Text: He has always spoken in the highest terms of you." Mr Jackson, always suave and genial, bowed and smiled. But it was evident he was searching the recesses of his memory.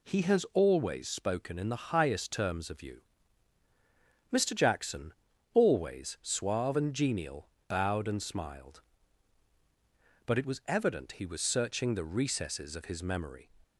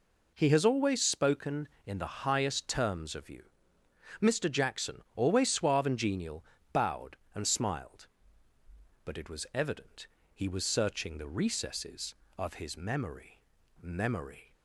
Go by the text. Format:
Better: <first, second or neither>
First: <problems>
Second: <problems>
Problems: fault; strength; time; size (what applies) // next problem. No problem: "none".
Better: first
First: none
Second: pauses between "evident" and "he"; slight; at 10.0 s; 0.26 s long // says "memory" twice; at 13.8 s